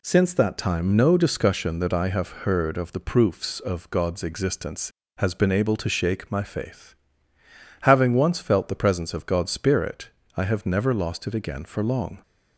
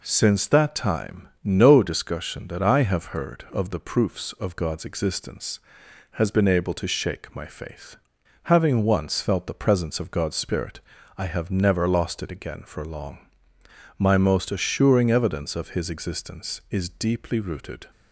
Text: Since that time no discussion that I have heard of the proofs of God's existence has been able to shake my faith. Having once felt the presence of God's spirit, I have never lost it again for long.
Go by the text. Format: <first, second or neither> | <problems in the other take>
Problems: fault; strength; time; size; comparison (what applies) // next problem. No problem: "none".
first | pauses between "time" and "no"; slight; at 1.2 s; 0.16 s long // goes on to say "My most assuring evidence of his existence is deeply rooted"; strong; from 13.9 s on; 3.9 s long